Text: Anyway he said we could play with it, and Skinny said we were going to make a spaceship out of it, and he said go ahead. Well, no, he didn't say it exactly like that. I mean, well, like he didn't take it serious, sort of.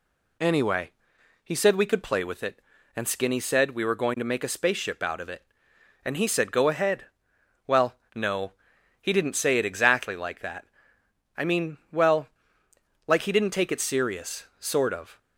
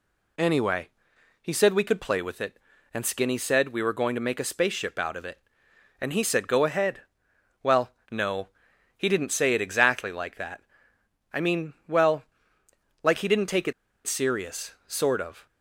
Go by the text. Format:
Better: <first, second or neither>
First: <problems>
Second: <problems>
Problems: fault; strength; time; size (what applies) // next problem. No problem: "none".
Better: first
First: pauses between "Anyway" and "he"; noticeable; at 0.9 s; 0.54 s long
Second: pauses between "Anyway" and "he"; noticeable; at 0.8 s; 0.54 s long // pauses between "it" and "serious"; slight; at 13.7 s; 0.34 s long